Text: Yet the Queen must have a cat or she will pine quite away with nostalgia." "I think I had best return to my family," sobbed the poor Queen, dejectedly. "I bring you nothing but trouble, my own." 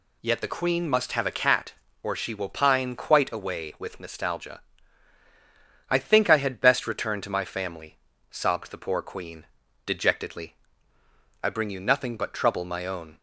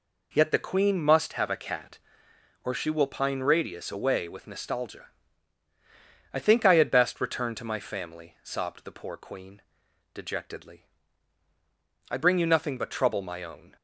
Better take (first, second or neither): first